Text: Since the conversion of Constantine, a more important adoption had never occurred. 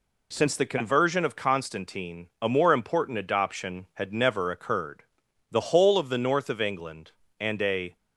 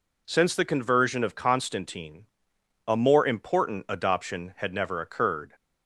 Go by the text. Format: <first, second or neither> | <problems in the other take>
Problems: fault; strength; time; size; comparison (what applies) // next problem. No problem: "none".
second | goes on to say "The whole of the north of England and a"; strong; from 5.4 s on; 2.4 s long